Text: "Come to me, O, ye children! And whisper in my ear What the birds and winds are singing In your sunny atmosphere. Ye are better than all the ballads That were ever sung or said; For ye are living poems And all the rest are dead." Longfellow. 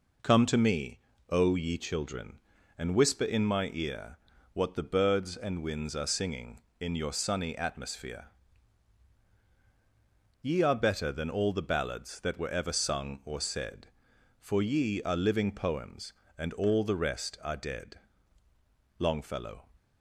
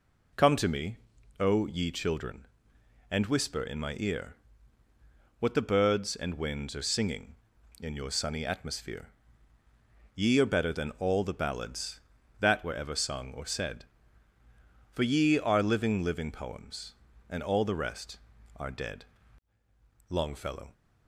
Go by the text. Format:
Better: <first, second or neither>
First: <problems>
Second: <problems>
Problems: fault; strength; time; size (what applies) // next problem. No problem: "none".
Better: first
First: pauses between "ear" and "What"; slight; at 4.1 s; 0.34 s long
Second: pauses between "ear" and "What"; at 4.3 s; 1.0 s long // says "living" twice; at 16.0 s